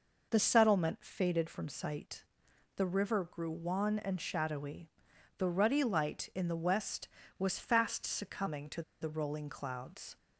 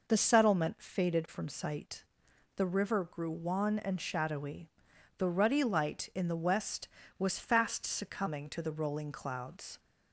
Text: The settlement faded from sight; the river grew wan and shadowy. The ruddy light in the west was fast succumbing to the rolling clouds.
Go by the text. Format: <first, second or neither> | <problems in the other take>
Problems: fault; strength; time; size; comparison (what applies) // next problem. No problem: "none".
second | pauses between "to" and "the"; slight; at 8.8 s; 0.20 s long